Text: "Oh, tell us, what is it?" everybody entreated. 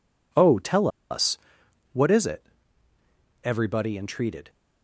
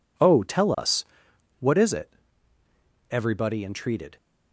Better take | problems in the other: second | pauses between "tell" and "us"; slight; at 0.8 s; 0.23 s long

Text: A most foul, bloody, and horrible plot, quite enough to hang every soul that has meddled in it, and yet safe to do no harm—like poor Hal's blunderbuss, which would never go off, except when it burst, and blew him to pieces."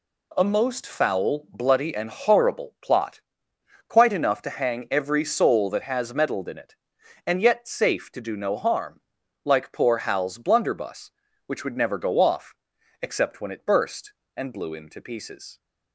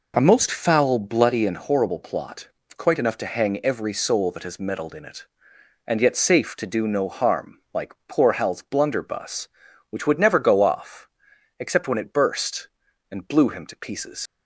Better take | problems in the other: first | leaves "pieces" unfinished; at 14.2 s; 95 ms

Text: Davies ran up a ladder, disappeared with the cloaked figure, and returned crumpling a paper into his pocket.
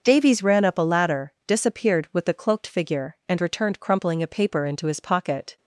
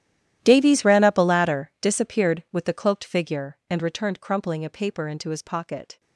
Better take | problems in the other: first | gets quieter; strong; throughout; 20.5 dB // starts louder than the rest; strong; until 1.4 s; 12 dB; noticeable in the first

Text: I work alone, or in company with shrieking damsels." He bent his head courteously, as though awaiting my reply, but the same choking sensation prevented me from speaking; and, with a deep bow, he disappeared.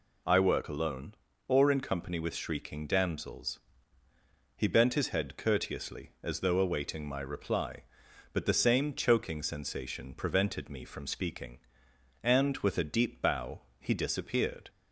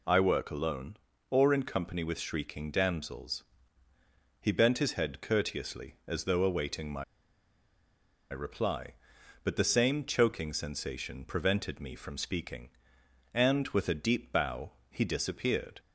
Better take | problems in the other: first | pauses between "my" and "reply"; strong; at 7.0 s; 1.2 s long

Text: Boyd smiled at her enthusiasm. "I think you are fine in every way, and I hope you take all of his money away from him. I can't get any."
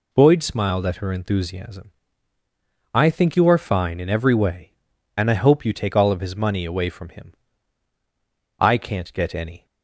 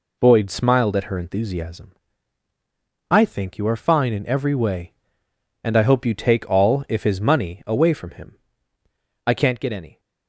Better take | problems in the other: first | says "if" for "of"; at 6.8 s

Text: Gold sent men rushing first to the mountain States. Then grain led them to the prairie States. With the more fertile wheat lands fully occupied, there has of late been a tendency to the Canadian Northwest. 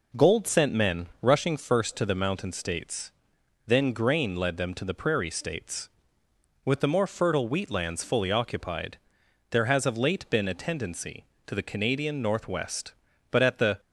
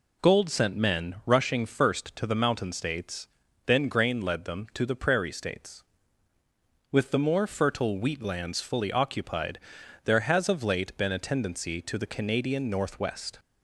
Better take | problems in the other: second | pauses between "men" and "rushing"; slight; at 1.0 s; 0.16 s long // goes on to say "But at the"; from 13.2 s on; 0.50 s long

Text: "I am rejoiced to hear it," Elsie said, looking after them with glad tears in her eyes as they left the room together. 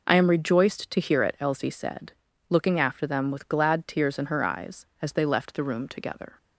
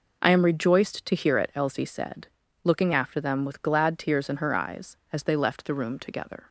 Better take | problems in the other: neither | none

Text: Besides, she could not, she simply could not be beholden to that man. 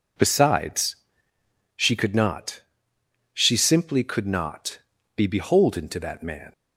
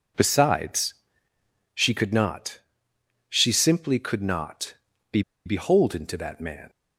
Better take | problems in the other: first | pauses between "not" and "be"; slight; at 4.7 s; 0.36 s long; slight in the first // pauses between "be" and "beholden"; slight; at 5.2 s; 0.24 s long

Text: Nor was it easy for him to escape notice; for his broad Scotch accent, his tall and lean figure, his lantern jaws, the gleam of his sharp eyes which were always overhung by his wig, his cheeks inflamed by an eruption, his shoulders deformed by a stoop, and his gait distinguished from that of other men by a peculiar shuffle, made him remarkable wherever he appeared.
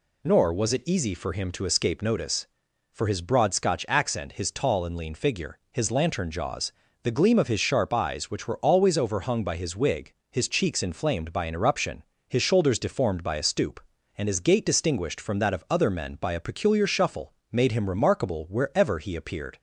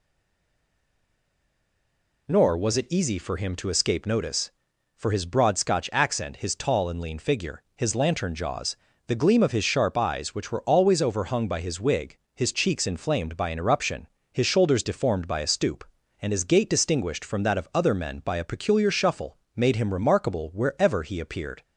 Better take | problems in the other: first | stays silent before the first word; until 2.2 s; 2.2 s long

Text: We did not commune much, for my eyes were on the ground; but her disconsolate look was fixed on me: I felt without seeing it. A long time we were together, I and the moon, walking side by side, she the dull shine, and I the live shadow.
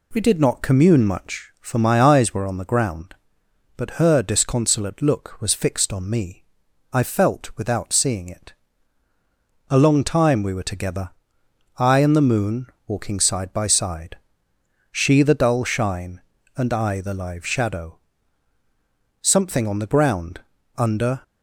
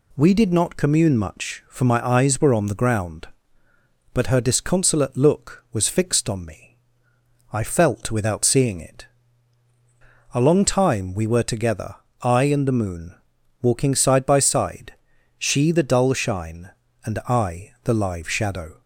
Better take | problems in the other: second | goes on to say "Something on the ground under"; strong; from 19.2 s on; 2.0 s long

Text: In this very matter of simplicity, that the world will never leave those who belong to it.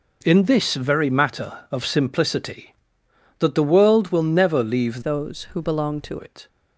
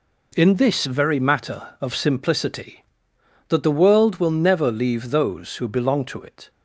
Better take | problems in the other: second | changes voice from "those" to "to"; from 5.0 to 6.1 s; 1.1 s long

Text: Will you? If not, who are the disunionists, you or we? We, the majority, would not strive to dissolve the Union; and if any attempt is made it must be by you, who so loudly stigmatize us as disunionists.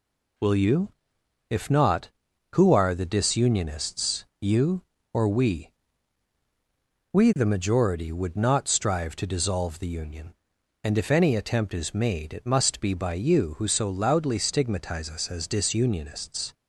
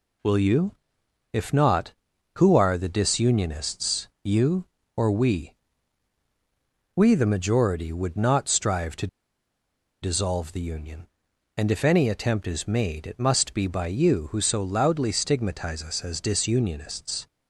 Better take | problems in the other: first | pauses between "to" and "dissolve"; noticeable; at 9.0 s; 0.94 s long

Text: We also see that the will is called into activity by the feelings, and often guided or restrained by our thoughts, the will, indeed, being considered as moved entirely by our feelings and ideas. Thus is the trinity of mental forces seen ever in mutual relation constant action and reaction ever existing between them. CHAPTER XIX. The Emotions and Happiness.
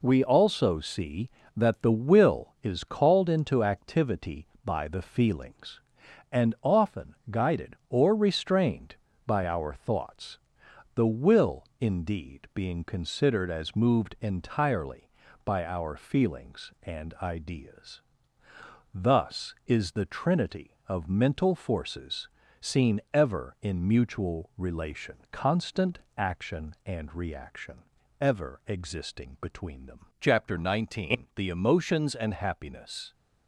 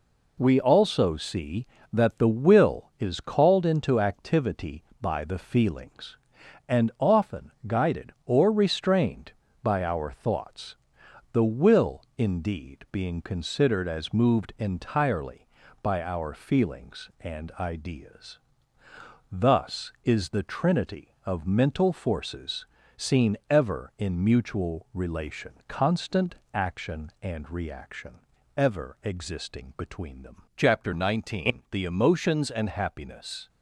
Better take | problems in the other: neither | pauses between "often" and "guided"; slight; the same in both // pauses between "forces" and "seen"; slight; the same in both // pauses between "relation" and "constant"; slight; the same in both // pauses between "constant" and "action"; slight; the same in both // pauses between "reaction" and "ever"; the same in both

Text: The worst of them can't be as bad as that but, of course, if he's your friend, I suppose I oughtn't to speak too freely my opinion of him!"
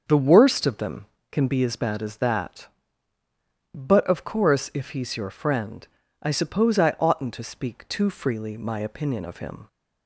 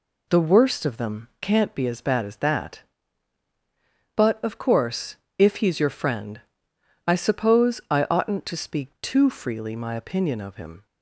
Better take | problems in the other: second | starts louder than the rest; until 1.3 s; 6.5 dB // says "can" for "can't"; at 1.3 s

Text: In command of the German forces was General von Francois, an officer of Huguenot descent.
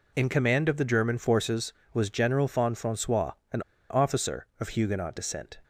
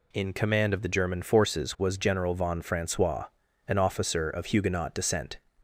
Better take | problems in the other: second | pauses between "an" and "officer"; slight; at 3.6 s; 0.28 s long

